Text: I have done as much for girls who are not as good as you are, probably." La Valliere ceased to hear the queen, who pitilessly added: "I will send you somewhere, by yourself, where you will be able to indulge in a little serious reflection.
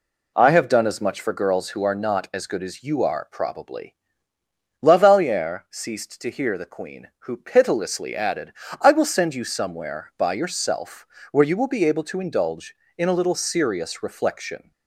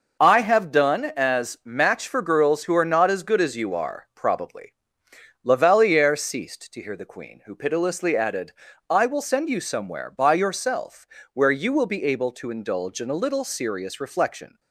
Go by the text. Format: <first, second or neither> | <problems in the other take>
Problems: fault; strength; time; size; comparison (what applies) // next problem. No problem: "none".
first | says "match" for "much"; at 1.6 s